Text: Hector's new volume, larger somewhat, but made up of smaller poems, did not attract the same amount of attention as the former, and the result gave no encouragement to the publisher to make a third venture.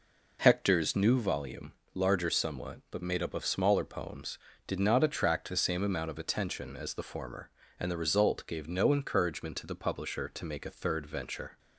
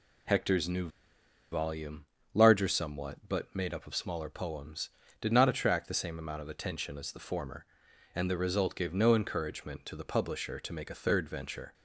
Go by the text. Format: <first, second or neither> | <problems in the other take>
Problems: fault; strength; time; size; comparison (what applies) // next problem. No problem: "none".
first | pauses between "new" and "volume"; noticeable; at 0.8 s; 0.63 s long